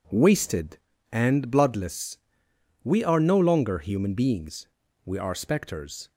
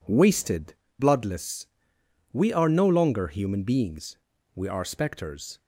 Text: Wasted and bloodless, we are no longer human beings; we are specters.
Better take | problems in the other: first | skips "and"; at 0.8 s

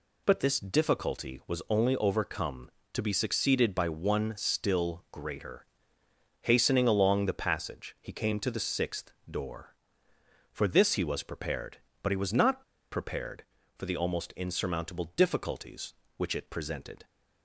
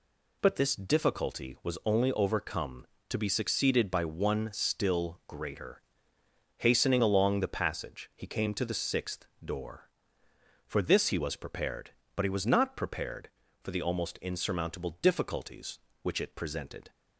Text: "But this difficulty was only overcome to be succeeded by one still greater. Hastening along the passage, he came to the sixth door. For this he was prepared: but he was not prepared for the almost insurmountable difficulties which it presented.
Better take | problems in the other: second | pauses between "sixth" and "door"; slight; at 9.1 s; 0.18 s long; slight in the second // pauses between "not" and "prepared"; slight; at 12.6 s; 0.28 s long

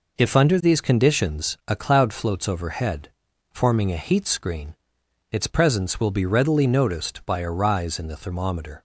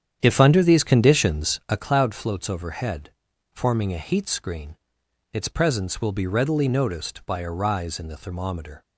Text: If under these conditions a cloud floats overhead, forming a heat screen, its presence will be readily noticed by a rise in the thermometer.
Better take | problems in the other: first | starts louder than the rest; strong; until 1.9 s; 9 dB

